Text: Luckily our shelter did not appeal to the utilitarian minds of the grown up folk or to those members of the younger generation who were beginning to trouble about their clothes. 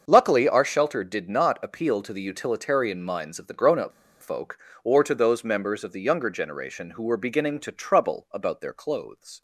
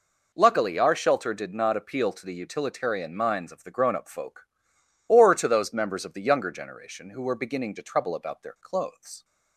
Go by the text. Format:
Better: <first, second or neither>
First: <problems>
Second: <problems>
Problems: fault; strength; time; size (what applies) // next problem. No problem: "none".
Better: second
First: starts louder than the rest; until 1.0 s; 6.5 dB // pauses between "up" and "folk"; slight; at 3.9 s; 0.29 s long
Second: none